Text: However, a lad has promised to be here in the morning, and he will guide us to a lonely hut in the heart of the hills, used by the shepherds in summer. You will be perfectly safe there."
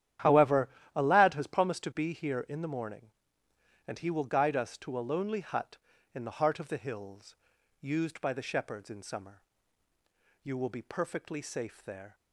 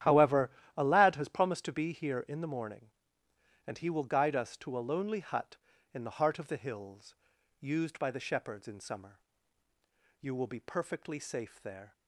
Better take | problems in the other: neither | starts louder than the rest; strong; the same in both

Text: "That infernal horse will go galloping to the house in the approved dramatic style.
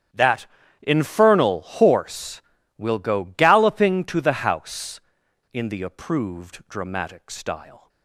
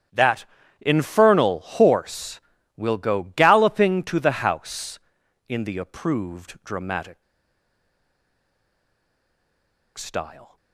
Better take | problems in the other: first | starts louder than the rest; strong; until 1.4 s; 10 dB; strong in the first // pauses between "That" and "infernal"; slight; at 0.4 s; 0.34 s long; slight in the first // pauses between "dramatic" and "style"; strong; at 7.2 s; 2.7 s long

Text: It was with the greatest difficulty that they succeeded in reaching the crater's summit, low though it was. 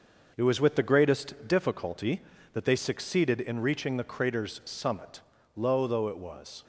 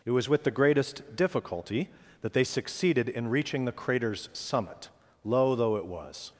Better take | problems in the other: second | gets quieter; noticeable; throughout; 4.5 dB

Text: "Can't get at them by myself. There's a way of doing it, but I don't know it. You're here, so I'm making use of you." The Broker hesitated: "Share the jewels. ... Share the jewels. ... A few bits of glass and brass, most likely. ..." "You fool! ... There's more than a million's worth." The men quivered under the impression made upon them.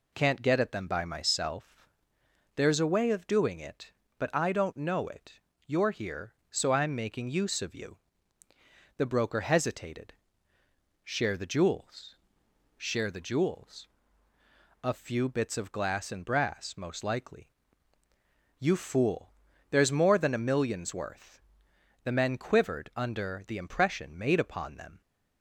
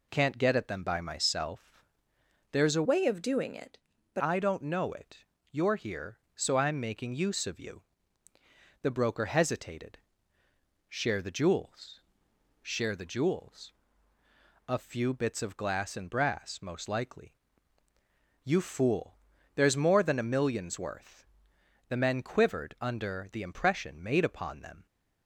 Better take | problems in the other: first | changes voice from "way" to "but"; from 2.8 to 4.2 s; 1.4 s long

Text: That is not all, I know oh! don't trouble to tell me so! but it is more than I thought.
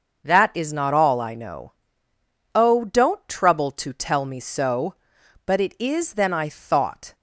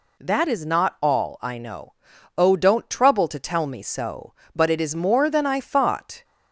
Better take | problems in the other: second | starts louder than the rest; noticeable; until 1.2 s; 6 dB // pauses between "know" and "oh"; noticeable; at 1.7 s; 0.82 s long; also in the second // skips "more"; at 6.1 s

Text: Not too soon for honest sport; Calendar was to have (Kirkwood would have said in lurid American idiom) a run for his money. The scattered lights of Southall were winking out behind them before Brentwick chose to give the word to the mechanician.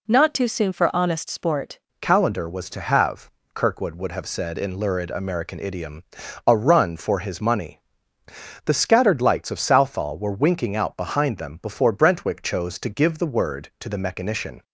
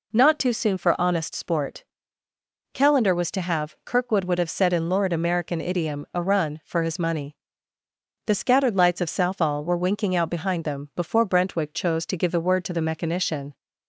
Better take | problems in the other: second | changes voice at "Calendar"; from 2.0 s on; 12.6 s long

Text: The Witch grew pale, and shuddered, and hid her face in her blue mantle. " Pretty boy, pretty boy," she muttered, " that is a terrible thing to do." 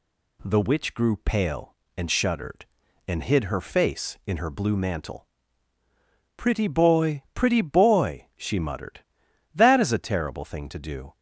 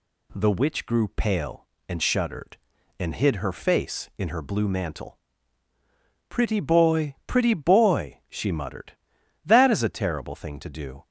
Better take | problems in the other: neither | none

